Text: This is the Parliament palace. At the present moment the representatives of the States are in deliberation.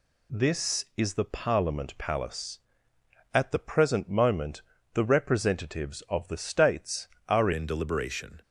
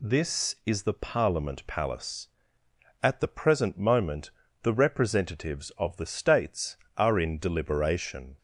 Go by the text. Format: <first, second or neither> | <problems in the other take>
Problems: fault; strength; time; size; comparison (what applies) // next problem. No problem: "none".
second | pauses between "moment" and "the"; slight; at 4.6 s; 0.32 s long; slight in the second // changes voice at "in"; from 7.5 s on; 0.9 s long